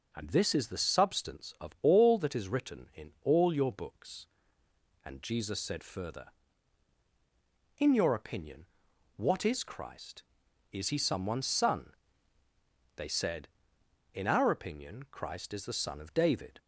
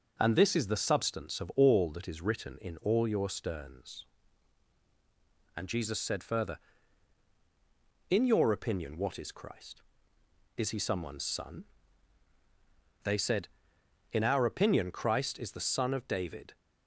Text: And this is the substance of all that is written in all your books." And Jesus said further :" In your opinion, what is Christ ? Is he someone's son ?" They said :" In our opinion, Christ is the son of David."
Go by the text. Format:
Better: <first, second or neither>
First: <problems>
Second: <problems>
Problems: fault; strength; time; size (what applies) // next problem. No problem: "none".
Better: first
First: starts louder than the rest; until 1.1 s; 6.5 dB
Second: starts louder than the rest; until 1.2 s; 6.5 dB // says "sterns" for "books"; at 3.2 s